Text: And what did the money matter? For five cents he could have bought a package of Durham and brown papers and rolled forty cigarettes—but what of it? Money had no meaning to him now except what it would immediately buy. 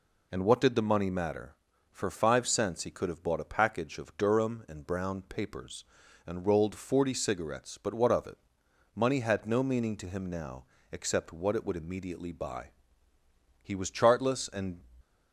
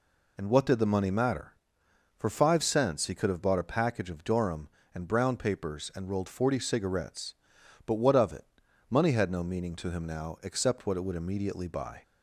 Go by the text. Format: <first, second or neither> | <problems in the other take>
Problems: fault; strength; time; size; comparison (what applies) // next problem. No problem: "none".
second | pauses between "now" and "except"; slight; at 10.6 s; 0.26 s long // goes on to say "He was chartless and"; noticeable; from 13.6 s on; 1.1 s long